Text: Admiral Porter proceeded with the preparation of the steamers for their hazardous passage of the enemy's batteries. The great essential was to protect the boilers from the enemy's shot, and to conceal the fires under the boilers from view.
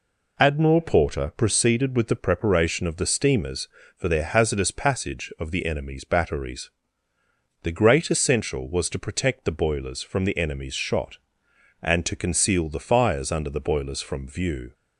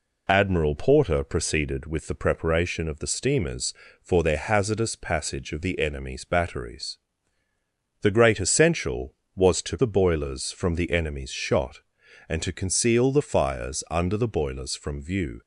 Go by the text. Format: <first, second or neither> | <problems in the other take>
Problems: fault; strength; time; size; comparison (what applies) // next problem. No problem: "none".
first | skips "protect"; at 9.7 s